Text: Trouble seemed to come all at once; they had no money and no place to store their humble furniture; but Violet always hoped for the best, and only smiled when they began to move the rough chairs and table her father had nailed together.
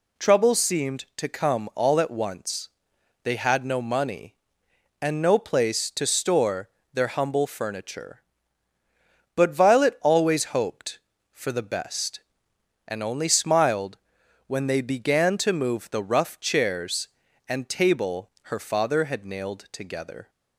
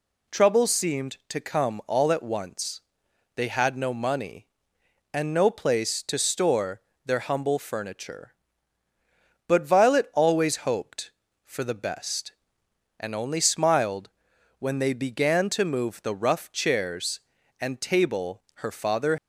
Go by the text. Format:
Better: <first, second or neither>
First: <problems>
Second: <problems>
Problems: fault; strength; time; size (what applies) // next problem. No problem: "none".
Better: first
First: pauses between "store" and "their"; slight; at 6.6 s; 0.24 s long // pauses between "smiled" and "when"; noticeable; at 13.9 s; 0.50 s long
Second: pauses between "store" and "their"; slight; at 6.8 s; 0.24 s long // pauses between "smiled" and "when"; noticeable; at 14.0 s; 0.50 s long // stops before "had nailed together"; at 19.1 s